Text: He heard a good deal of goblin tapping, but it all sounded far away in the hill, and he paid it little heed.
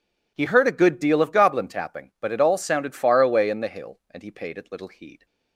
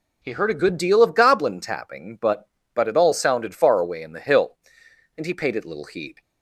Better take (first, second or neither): first